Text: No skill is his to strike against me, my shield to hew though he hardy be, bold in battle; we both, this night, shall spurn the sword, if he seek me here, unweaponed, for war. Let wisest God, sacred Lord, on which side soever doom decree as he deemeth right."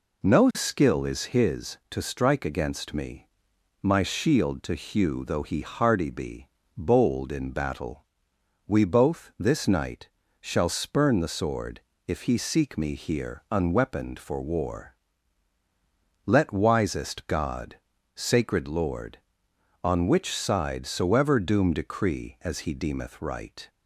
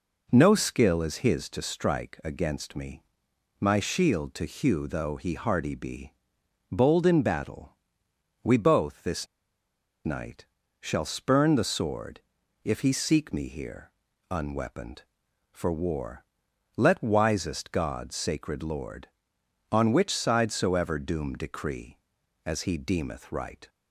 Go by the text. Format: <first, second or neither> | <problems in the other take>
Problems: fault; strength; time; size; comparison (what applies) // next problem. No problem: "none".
first | pauses between "this" and "night"; noticeable; at 9.2 s; 0.78 s long